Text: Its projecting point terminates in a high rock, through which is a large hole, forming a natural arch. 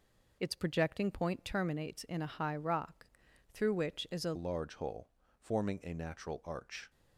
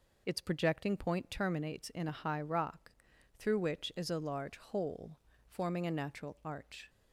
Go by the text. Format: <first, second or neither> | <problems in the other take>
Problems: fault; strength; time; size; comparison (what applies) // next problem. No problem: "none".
second | changes voice at "large"; from 4.3 s on; 2.5 s long